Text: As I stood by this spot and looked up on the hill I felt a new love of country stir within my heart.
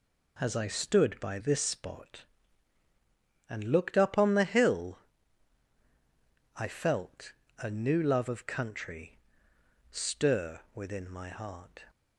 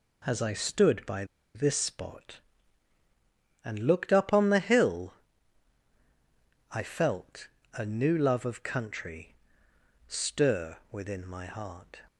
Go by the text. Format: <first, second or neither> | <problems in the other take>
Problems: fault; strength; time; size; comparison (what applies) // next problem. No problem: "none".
first | pauses between "by" and "this"; slight; at 1.2 s; 0.29 s long // pauses between "hill" and "I"; strong; at 5.1 s; 1.6 s long; strong in the first // pauses between "felt" and "a"; slight; at 7.4 s; 0.28 s long; slight in the first // pauses between "country" and "stir"; noticeable; at 9.3 s; 0.74 s long; noticeable in the first